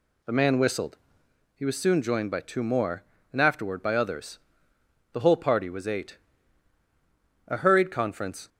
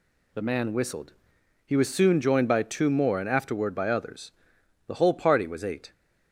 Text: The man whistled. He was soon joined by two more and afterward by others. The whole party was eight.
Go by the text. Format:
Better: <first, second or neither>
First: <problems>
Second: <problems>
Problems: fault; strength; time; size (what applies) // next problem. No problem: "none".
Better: second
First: goes on to say "A hurried conference"; noticeable; from 7.4 s on; 1.0 s long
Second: none